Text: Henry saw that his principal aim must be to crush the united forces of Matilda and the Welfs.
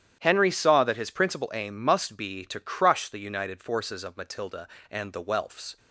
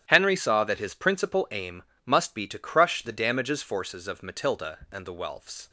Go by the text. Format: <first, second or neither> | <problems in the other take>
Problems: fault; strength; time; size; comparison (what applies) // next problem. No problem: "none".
first | starts louder than the rest; strong; until 1.0 s; 11 dB; strong in the first // pauses between "aim" and "must"; slight; at 1.8 s; 0.24 s long // says "damages" for "united"; at 3.1 s